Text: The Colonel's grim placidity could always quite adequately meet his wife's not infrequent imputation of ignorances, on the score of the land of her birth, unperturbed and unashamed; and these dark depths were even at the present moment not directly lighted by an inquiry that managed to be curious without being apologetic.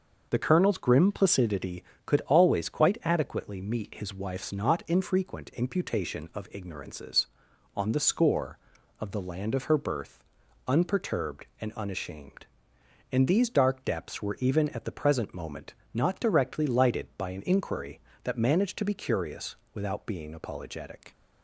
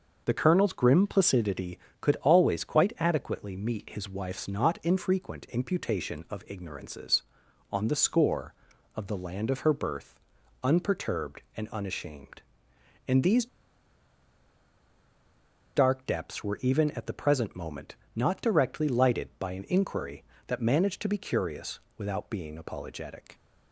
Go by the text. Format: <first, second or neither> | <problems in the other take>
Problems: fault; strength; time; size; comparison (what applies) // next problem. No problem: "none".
first | starts louder than the rest; until 1.2 s; 6 dB; also in the first // pauses between "these" and "dark"; strong; at 13.4 s; 2.2 s long // pauses between "moment" and "not"; slight; at 17.9 s; 0.18 s long; slight in the first // pauses between "curious" and "without"; slight; at 21.8 s; 0.18 s long; slight in the first